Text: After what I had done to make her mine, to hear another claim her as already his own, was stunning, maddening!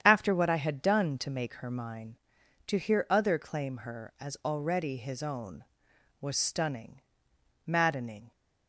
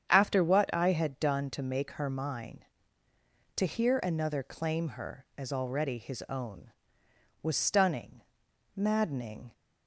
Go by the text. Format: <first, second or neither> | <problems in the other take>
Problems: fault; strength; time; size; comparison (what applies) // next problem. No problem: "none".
second | starts louder than the rest; strong; until 1.0 s; 9 dB; strong in the second // says "other" for "another"; at 3.0 s